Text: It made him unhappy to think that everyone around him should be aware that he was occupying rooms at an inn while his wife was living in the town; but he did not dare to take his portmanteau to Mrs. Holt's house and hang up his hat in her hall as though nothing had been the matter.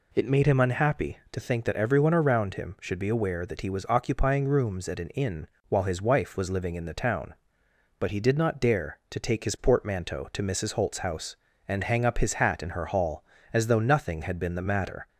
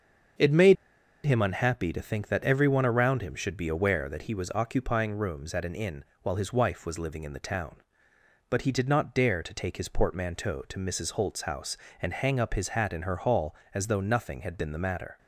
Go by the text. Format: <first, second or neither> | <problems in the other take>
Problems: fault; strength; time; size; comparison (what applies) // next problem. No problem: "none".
first | starts louder than the rest; until 1.8 s; 7 dB // pauses between "made" and "him"; noticeable; at 0.7 s; 0.50 s long // pauses between "inn" and "while"; slight; at 6.0 s; 0.18 s long; slight in the first